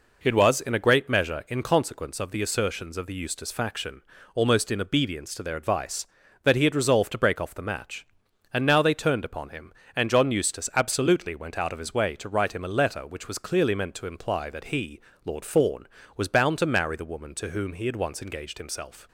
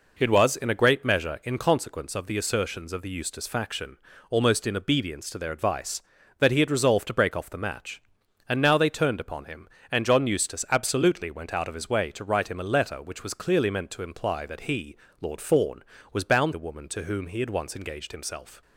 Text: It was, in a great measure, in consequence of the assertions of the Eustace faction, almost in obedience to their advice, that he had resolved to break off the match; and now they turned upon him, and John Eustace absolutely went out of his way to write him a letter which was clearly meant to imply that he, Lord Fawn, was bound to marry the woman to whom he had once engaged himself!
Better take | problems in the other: first | skips "to marry"; at 16.5 s

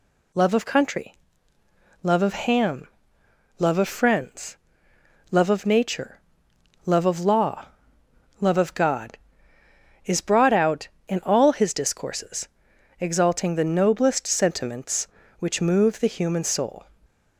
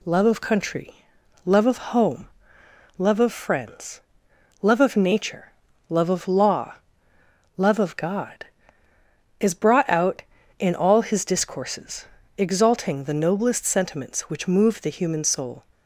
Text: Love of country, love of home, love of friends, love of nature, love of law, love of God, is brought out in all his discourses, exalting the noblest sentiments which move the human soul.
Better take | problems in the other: second | says "ham" for "home"; at 2.3 s

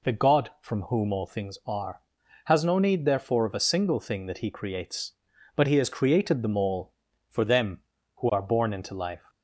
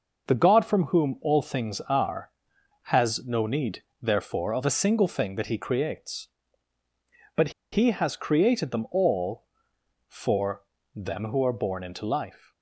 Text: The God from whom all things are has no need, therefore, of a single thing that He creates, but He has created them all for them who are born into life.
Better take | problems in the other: first | pauses between "but" and "He"; slight; at 7.4 s; 0.22 s long // pauses between "for" and "them"; slight; at 10.6 s; 0.32 s long

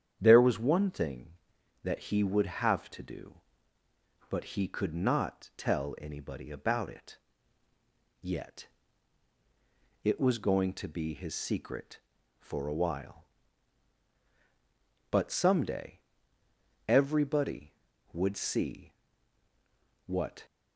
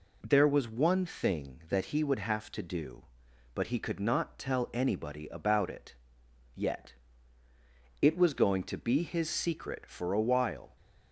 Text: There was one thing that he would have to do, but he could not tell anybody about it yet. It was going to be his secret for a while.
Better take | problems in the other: second | starts louder than the rest; strong; until 1.2 s; 8.5 dB // pauses between "it" and "yet"; at 7.1 s; 1.0 s long; noticeable in the second // goes on to say "But someday everybody would see what"; strong; from 15.1 s on; 5.3 s long

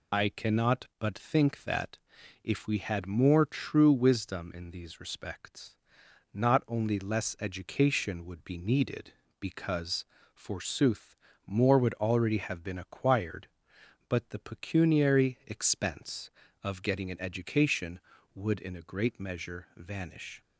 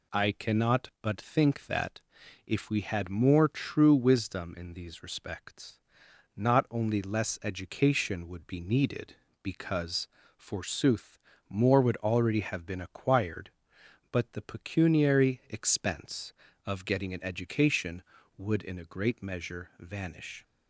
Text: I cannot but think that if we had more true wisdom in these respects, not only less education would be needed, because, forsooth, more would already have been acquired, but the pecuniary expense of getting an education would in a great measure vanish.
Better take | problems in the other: second | loses the start of "I"; at 0.1 s; 40 ms // pauses between "that" and "if"; noticeable; at 1.9 s; 0.46 s long; noticeable in the second

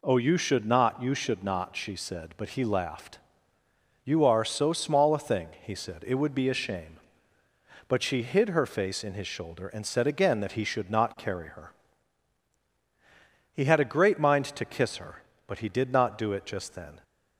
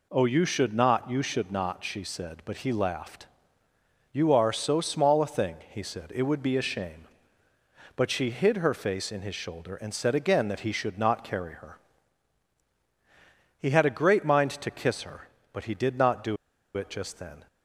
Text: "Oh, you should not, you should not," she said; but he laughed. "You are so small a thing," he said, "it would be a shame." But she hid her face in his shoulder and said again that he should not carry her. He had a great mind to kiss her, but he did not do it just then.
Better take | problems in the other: first | pauses between "do" and "it"; at 16.3 s; 0.40 s long

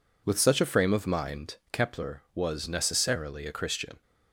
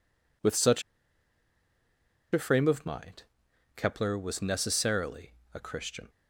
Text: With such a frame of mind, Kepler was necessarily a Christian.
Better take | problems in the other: first | pauses between "such" and "a"; strong; at 0.8 s; 1.5 s long // pauses between "necessarily" and "a"; slight; at 5.3 s; 0.22 s long

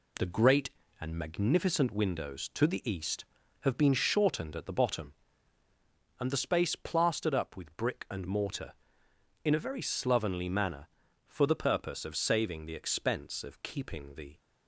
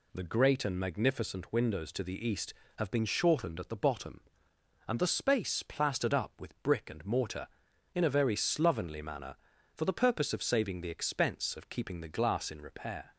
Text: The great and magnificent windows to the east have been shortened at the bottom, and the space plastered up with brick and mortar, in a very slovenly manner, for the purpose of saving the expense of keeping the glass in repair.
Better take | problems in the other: second | stops before "glass in repair"; at 14.3 s

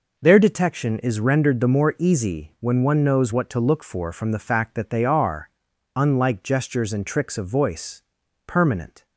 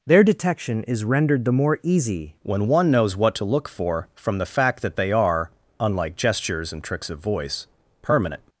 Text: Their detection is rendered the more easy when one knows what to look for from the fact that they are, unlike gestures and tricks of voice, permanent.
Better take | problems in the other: first | changes voice at "when"; from 2.4 s on; 6.0 s long

